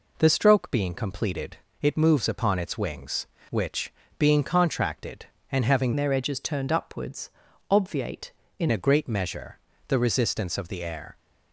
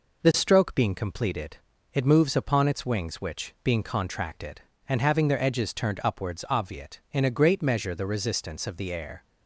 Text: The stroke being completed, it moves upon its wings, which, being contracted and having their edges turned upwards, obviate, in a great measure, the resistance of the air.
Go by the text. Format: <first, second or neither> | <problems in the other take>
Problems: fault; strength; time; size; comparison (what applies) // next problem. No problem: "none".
second | changes voice from "their" to "in"; from 5.9 to 8.6 s; 2.7 s long